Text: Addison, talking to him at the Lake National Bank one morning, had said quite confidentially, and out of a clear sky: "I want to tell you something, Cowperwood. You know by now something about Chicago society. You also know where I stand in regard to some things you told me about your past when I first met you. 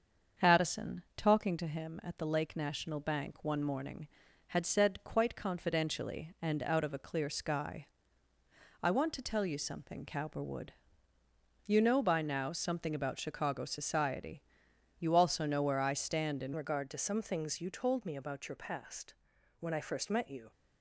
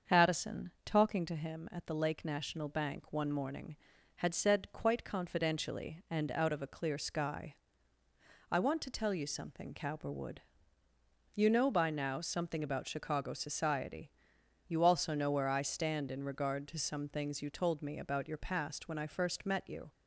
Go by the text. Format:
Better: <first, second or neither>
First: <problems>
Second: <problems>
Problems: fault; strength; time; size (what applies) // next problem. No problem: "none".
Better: second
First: starts louder than the rest; until 1.5 s; 7 dB // changes voice at "regard"; from 16.5 s on; 4.0 s long // pauses between "past" and "when"; noticeable; at 19.1 s; 0.46 s long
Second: starts louder than the rest; until 1.2 s; 7 dB